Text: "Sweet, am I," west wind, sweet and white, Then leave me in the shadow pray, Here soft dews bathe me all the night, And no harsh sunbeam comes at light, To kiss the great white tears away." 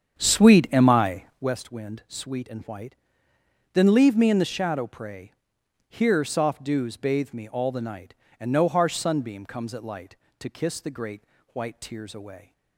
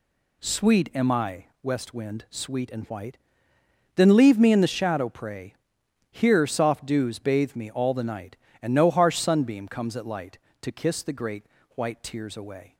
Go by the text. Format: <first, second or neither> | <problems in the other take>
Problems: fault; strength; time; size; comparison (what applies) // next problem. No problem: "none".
second | starts louder than the rest; strong; until 1.6 s; 8 dB // pauses between "great" and "white"; slight; at 11.2 s; 0.28 s long; slight in the second